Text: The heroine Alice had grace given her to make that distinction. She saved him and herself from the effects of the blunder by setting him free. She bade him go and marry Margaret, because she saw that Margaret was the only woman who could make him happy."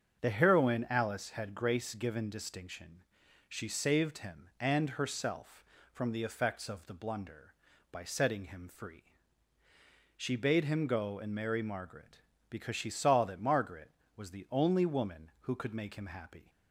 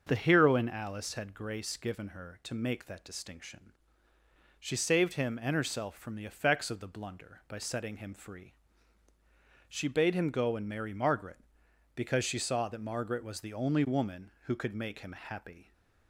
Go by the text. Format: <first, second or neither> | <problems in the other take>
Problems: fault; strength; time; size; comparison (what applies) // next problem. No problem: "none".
second | starts louder than the rest; until 1.2 s; 7 dB; also in the second // skips "her to make that"; at 2.3 s